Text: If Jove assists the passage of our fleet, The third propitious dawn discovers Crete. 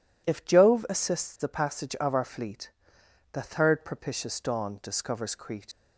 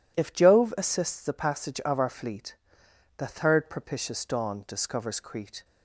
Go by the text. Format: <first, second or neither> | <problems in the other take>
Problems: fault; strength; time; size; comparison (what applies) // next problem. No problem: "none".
second | leaves "Crete" unfinished; at 5.7 s; 80 ms